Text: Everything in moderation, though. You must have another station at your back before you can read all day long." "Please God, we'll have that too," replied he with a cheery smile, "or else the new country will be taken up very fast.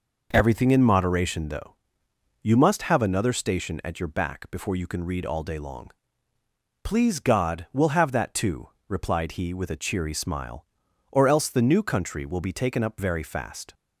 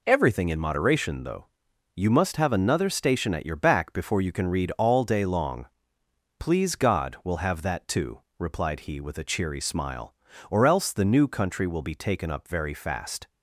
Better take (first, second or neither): neither